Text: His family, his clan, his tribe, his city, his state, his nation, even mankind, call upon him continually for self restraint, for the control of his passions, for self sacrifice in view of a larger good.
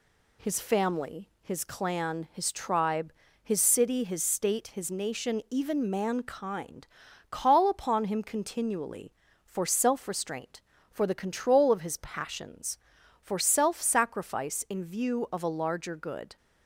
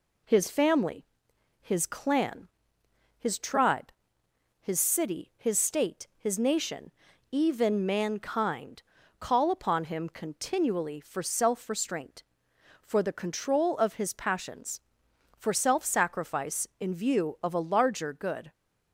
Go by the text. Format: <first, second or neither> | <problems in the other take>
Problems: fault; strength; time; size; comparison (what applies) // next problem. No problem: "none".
neither | none